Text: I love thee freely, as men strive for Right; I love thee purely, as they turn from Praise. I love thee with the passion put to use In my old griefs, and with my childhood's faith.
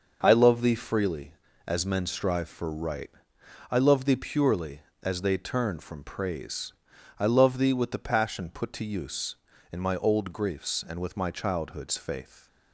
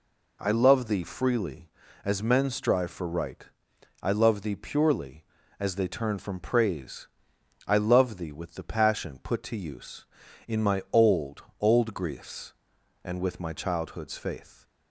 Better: first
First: none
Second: says "old" twice; at 11.5 s

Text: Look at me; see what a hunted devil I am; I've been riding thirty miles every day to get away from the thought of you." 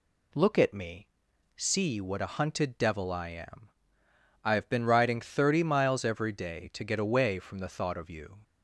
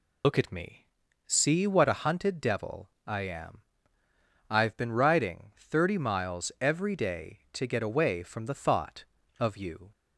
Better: first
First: none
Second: loses the start of "Look"; at 0.2 s; 105 ms // pauses between "devil" and "I"; slight; at 2.8 s; 0.18 s long

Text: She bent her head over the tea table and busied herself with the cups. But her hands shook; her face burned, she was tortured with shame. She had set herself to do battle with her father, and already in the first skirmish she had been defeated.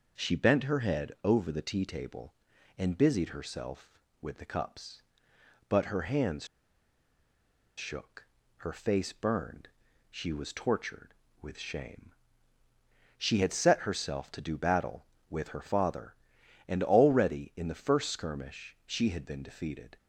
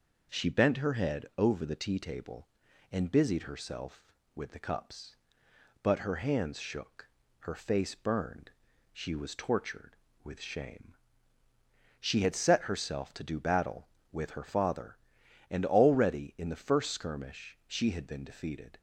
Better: second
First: pauses between "hands" and "shook"; strong; at 6.4 s; 1.3 s long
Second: none

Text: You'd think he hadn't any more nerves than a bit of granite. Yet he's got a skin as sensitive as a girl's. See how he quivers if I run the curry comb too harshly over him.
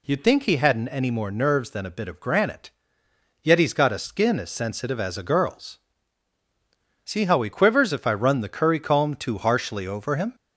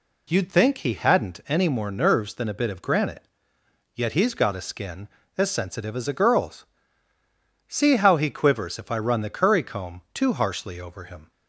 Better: neither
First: none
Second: none

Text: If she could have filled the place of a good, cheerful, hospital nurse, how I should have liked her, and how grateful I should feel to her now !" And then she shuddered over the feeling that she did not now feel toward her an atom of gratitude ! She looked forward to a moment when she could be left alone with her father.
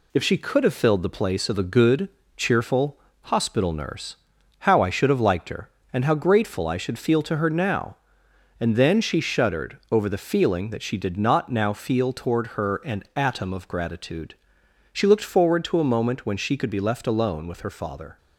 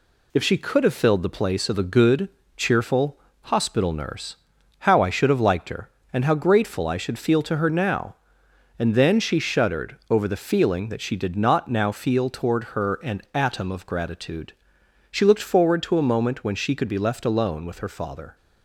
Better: neither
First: none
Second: none

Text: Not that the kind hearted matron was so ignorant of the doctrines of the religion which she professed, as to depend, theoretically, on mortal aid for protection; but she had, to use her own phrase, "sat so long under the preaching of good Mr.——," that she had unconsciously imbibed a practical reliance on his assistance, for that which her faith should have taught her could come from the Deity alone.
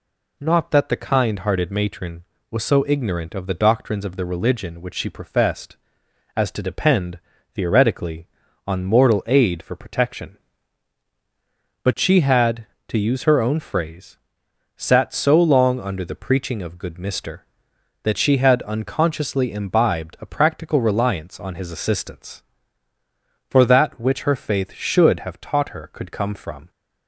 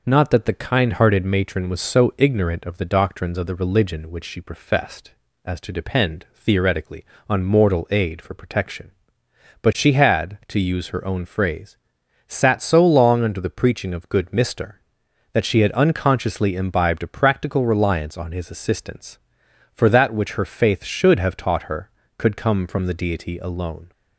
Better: second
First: stops before "the Deity alone"; at 26.7 s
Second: none

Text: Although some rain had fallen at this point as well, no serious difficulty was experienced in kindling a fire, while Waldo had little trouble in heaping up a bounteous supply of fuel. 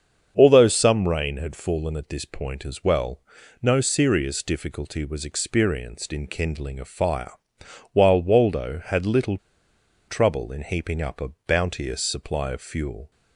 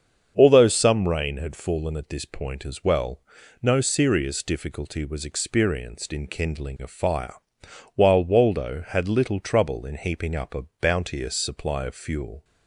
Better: second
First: starts louder than the rest; strong; until 1.3 s; 7 dB // pauses between "little" and "trouble"; noticeable; at 9.3 s; 0.70 s long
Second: starts louder than the rest; strong; until 1.3 s; 7 dB

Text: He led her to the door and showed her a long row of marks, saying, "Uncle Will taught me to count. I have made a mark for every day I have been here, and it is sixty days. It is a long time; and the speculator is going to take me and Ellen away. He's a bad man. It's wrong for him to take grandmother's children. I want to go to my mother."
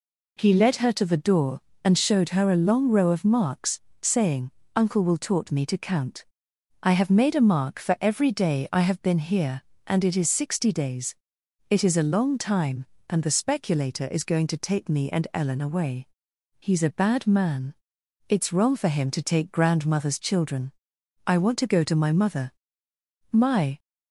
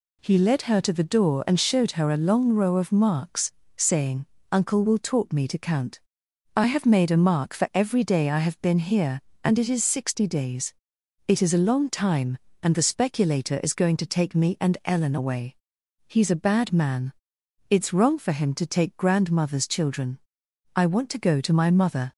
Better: second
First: goes on to say "My"; slight; from 23.3 s on; 0.48 s long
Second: none

